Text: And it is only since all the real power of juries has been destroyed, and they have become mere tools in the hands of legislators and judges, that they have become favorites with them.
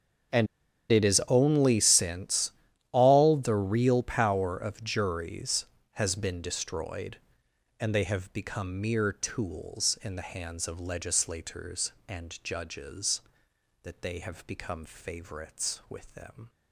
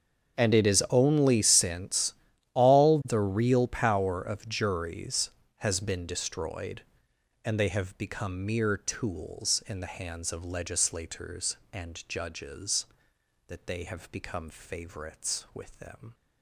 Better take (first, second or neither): second